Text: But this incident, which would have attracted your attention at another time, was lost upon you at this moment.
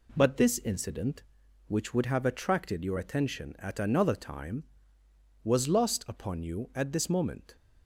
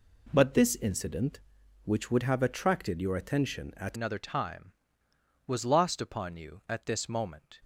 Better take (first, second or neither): first